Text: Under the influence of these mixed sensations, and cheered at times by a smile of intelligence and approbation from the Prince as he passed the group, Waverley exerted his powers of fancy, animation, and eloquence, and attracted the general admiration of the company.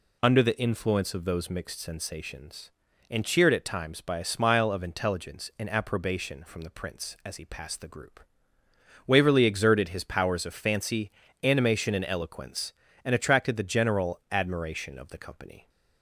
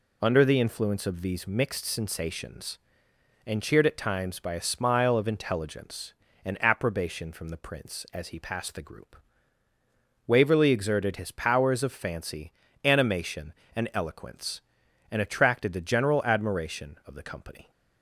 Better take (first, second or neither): second